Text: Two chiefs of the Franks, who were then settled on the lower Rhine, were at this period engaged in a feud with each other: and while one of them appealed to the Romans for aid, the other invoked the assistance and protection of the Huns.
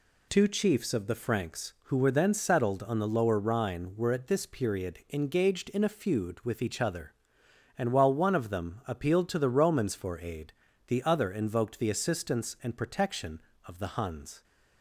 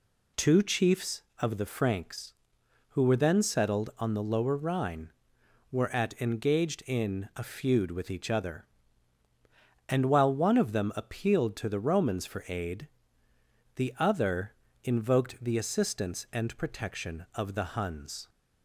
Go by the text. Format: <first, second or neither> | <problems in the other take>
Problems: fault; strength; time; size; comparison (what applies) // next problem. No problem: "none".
first | skips "this period"; at 6.1 s // pauses between "other" and "invoked"; slight; at 14.5 s; 0.28 s long